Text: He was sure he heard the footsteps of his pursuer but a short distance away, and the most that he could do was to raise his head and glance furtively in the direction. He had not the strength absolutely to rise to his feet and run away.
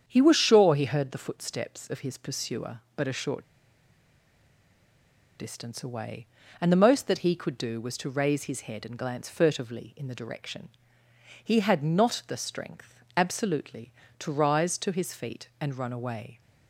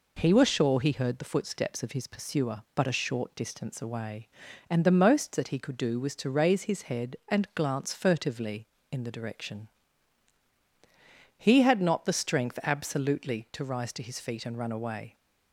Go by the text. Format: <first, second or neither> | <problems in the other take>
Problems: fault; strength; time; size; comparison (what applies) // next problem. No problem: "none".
second | starts louder than the rest; strong; until 1.0 s; 8 dB // pauses between "short" and "distance"; strong; at 3.4 s; 1.9 s long // pauses between "strength" and "absolutely"; slight; at 12.9 s; 0.22 s long